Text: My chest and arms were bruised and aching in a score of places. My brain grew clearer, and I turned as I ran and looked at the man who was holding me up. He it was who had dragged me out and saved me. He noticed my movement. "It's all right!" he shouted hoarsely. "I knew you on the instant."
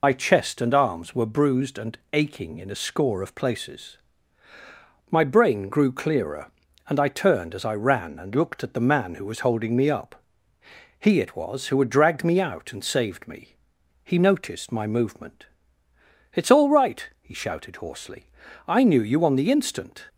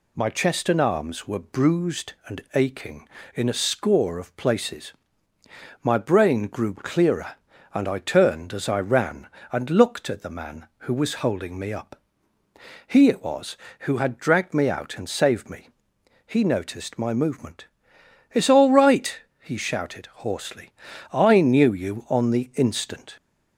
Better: second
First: loses the start of "My"; at 0.0 s; 50 ms // pauses between "and" and "aching"; slight; at 1.9 s; 0.16 s long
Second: none

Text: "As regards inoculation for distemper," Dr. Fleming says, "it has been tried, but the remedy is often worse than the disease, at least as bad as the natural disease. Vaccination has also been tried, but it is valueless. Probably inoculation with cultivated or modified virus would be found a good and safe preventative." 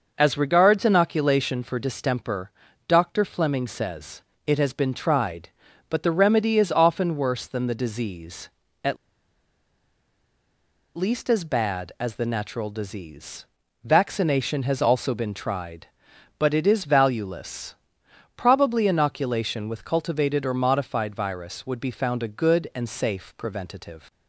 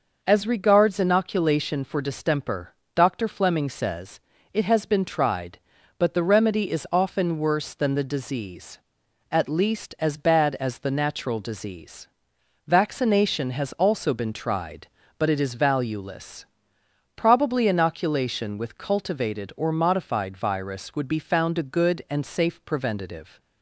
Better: second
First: starts louder than the rest; noticeable; until 1.1 s; 6 dB // pauses between "at" and "least"; strong; at 8.9 s; 2.0 s long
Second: none

